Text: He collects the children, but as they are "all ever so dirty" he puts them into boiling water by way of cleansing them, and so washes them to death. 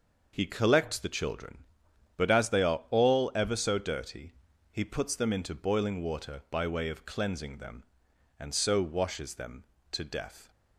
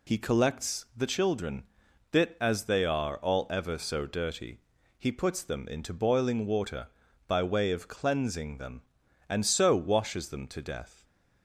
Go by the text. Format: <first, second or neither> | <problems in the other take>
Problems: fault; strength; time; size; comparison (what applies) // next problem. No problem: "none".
first | says "bit" for "but"; at 2.1 s // pauses between "dirty" and "he"; at 4.5 s; 0.38 s long; also in the first